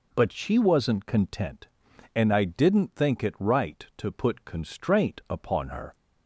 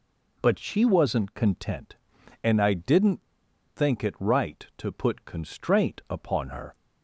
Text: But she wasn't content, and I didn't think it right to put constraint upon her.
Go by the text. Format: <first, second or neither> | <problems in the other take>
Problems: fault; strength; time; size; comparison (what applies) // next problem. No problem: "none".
first | pauses between "didn't" and "think"; noticeable; at 3.2 s; 0.52 s long